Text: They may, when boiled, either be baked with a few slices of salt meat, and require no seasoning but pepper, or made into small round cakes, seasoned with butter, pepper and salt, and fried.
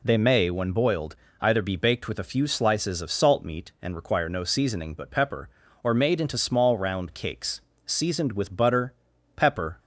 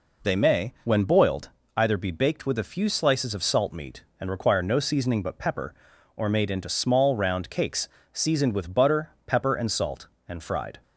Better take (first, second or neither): second